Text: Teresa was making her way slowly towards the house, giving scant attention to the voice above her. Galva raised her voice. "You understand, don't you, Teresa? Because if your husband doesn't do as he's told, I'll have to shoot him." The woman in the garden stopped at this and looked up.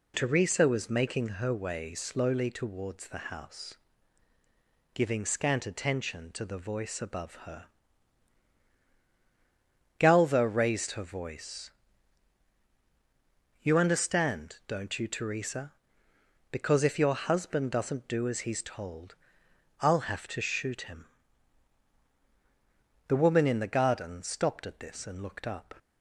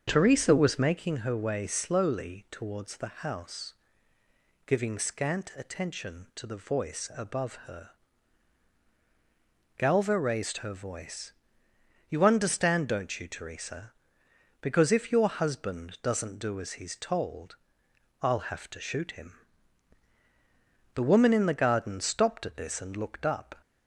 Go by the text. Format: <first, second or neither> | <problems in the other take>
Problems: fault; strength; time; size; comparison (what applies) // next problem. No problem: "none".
first | starts louder than the rest; strong; until 1.2 s; 7 dB